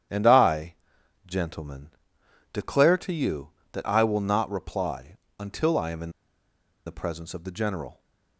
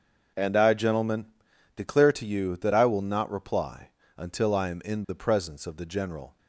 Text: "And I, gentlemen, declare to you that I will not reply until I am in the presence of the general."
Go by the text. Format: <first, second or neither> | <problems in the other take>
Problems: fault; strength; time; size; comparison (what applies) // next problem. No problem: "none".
second | starts louder than the rest; strong; until 1.6 s; 10 dB; also in the second // pauses between "reply" and "until"; slight; at 5.1 s; 0.20 s long; slight in the second // pauses between "in" and "the"; noticeable; at 6.1 s; 0.76 s long